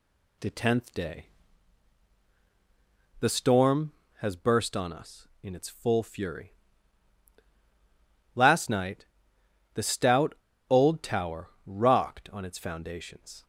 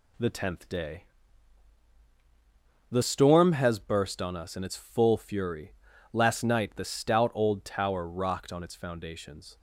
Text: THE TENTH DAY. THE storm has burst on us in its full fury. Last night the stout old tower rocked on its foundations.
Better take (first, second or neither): second